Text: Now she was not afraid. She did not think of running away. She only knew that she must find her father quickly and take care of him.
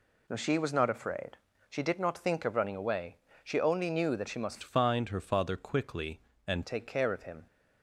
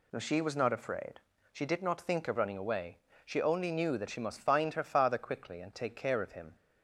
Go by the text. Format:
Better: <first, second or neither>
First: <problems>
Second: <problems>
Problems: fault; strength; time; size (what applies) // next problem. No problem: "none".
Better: second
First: changes voice from "find" to "and"; from 4.6 to 6.6 s; 2.0 s long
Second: none